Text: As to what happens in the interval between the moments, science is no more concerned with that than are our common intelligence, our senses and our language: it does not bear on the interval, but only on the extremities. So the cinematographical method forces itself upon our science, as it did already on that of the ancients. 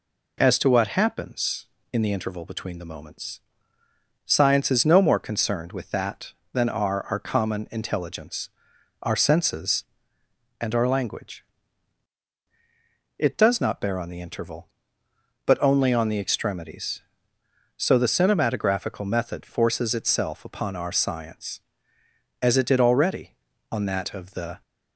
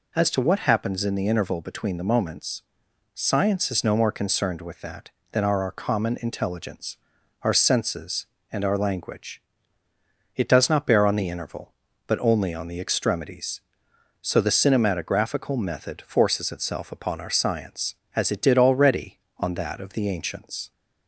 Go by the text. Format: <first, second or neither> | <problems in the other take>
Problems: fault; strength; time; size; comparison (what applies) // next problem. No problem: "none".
second | stops before "ancients"; at 24.6 s